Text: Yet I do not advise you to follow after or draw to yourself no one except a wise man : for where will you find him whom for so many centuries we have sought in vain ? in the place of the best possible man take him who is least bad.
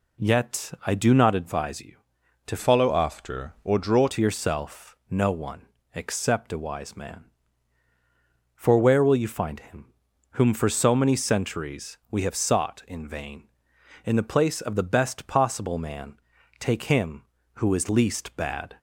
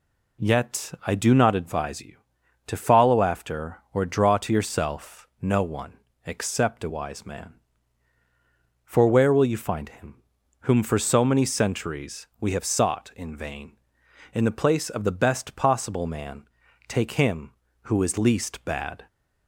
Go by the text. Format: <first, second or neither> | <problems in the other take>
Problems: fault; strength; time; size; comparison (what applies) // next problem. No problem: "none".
second | changes voice from "follow" to "draw"; from 2.5 to 4.0 s; 1.5 s long // pauses between "one" and "except"; slight; at 5.6 s; 0.28 s long; slight in the second // pauses between "him" and "whom"; at 9.9 s; 0.38 s long; also in the second // pauses between "man" and "take"; at 16.1 s; 0.44 s long; also in the second